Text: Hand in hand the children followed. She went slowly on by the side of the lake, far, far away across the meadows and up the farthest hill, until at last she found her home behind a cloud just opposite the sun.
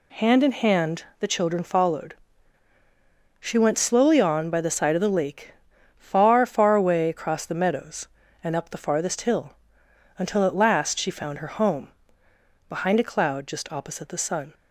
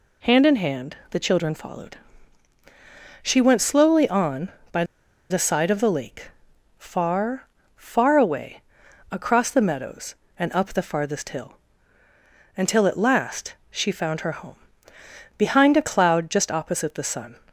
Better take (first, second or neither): first